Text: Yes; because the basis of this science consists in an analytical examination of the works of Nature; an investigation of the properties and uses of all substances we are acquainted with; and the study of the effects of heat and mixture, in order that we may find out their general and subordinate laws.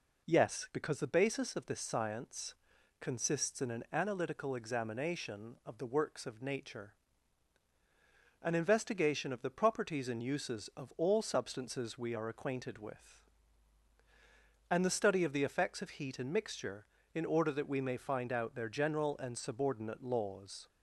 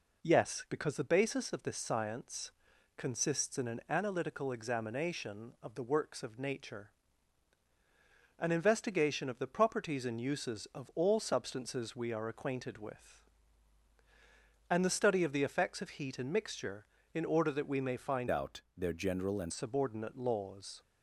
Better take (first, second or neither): first